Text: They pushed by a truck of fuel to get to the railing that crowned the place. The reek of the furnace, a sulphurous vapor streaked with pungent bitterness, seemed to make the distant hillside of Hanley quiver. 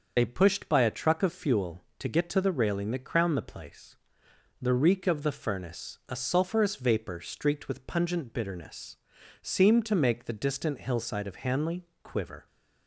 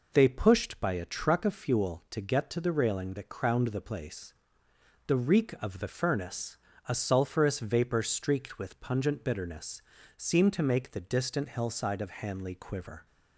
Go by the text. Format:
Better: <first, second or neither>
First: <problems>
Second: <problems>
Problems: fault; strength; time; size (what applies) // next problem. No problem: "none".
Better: second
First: loses the start of "They"; at 0.1 s; 50 ms // starts louder than the rest; until 1.1 s; 6 dB // pauses between "Hanley" and "quiver"; slight; at 11.8 s; 0.16 s long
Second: none